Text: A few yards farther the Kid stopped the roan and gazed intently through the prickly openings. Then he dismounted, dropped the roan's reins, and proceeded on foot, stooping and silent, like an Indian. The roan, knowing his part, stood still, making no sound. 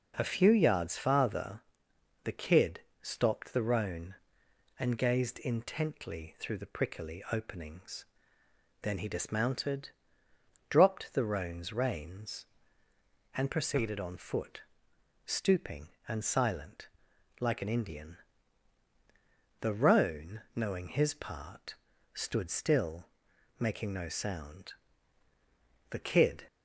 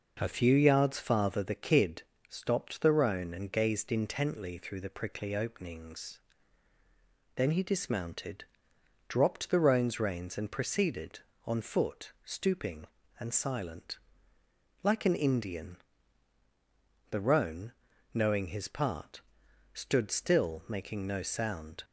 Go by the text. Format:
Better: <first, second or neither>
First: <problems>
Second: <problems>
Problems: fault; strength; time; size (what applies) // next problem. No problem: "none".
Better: second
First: pauses between "farther" and "the"; noticeable; at 1.6 s; 0.62 s long // pauses between "Kid" and "stopped"; slight; at 2.7 s; 0.24 s long // goes on to say "The Kid"; from 25.8 s on; 0.56 s long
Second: pauses between "Kid" and "stopped"; slight; at 2.0 s; 0.26 s long